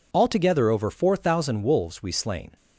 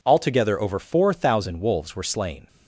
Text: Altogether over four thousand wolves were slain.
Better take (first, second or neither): second